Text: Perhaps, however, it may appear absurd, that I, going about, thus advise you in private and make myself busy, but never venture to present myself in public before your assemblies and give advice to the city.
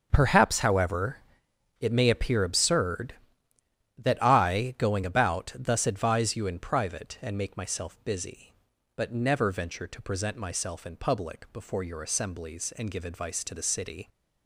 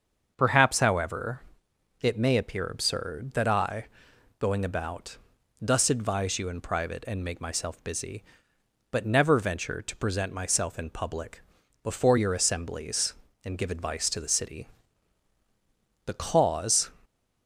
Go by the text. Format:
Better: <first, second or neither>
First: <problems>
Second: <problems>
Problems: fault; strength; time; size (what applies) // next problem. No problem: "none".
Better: first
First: starts louder than the rest; until 1.1 s; 7 dB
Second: starts louder than the rest; until 1.3 s; 6.5 dB // pauses between "public" and "before"; at 11.4 s; 0.42 s long // goes on to say "The cause"; noticeable; from 16.0 s on; 0.86 s long